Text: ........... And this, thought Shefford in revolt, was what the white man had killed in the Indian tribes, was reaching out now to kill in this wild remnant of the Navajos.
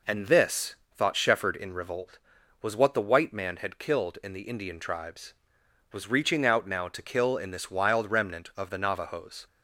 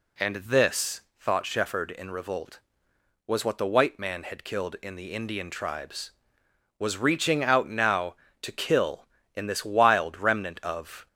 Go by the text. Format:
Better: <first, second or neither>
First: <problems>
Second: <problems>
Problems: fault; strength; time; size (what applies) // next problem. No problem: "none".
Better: first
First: none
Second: stops before "the Navajos"; at 11.0 s